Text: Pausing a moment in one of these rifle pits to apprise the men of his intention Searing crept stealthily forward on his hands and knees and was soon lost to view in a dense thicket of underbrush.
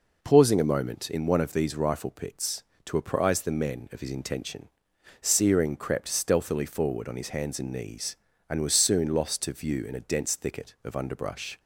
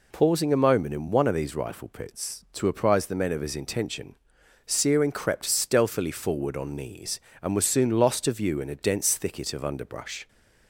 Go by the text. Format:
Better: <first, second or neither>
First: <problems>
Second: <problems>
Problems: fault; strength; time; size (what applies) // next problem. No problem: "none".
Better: first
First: pauses between "intention" and "Searing"; noticeable; at 4.6 s; 0.52 s long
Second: pauses between "intention" and "Searing"; noticeable; at 4.1 s; 0.54 s long // skips "his hands and"; at 6.7 s